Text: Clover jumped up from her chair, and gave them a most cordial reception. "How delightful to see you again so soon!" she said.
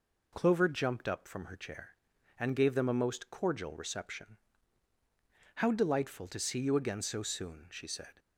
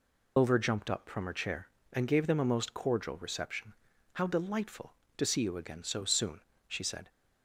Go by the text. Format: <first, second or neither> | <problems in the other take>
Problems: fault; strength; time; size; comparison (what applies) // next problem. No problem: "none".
first | loses the start of "Clover"; at 0.3 s; 140 ms